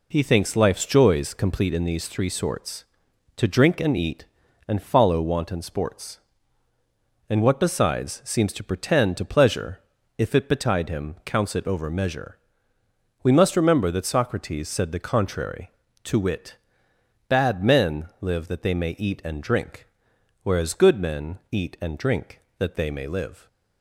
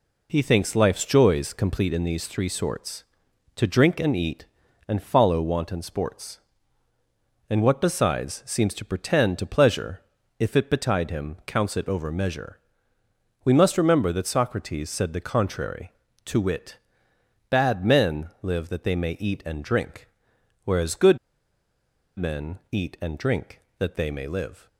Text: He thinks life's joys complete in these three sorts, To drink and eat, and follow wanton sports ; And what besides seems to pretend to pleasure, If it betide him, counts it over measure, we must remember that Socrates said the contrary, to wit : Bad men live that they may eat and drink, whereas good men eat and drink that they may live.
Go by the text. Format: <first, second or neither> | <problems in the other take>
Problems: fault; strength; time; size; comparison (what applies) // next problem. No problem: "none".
first | pauses between "good" and "men"; at 21.1 s; 1.0 s long